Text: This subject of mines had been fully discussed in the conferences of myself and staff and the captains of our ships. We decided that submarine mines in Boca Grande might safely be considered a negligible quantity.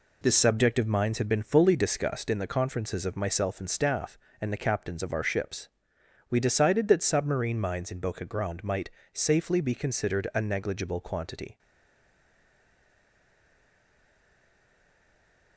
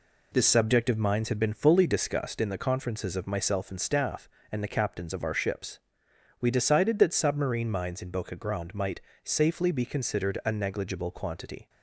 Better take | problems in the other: second | pauses between "might" and "safely"; slight; at 8.8 s; 0.24 s long; slight in the second // stays silent after the last word; strong; from 11.5 s on; 4.0 s long

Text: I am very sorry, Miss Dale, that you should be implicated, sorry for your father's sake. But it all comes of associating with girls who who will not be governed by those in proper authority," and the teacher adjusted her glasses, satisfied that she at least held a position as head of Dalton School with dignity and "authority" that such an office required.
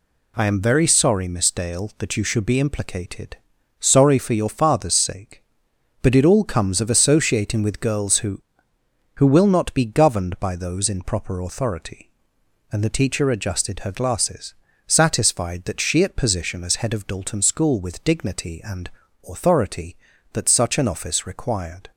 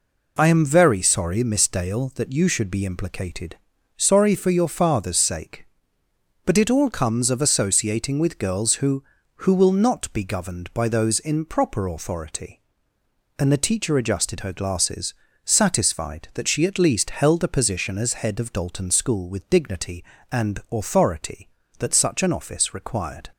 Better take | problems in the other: second | skips "least held a"; at 16.1 s // pauses between "and" and "authority"; at 18.8 s; 0.40 s long

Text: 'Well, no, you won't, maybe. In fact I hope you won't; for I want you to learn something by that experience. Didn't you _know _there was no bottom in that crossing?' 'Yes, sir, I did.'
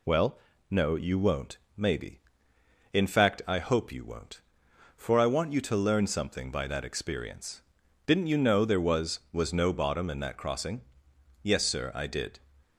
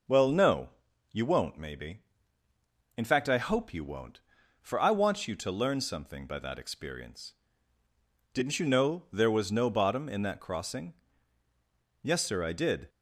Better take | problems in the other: second | says "was" twice; at 9.3 s

